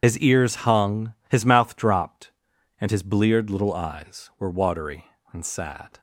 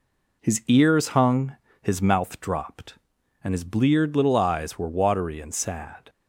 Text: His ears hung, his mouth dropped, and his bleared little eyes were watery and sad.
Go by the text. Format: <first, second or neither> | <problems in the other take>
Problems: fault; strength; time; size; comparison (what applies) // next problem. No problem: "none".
second | loses the start of "His"; at 0.0 s; 55 ms